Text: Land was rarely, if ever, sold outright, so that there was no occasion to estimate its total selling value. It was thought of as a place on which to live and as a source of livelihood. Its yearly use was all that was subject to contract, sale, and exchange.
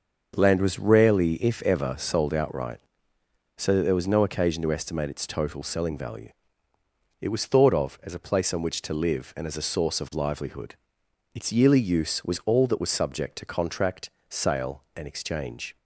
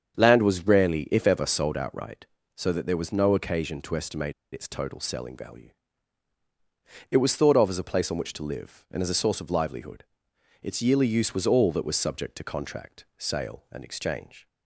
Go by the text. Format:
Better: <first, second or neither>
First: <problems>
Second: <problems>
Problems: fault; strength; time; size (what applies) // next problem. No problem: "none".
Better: first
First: starts louder than the rest; until 1.3 s; 6 dB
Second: starts louder than the rest; strong; until 1.1 s; 7.5 dB // pauses between "estimate" and "its"; slight; at 4.3 s; 0.20 s long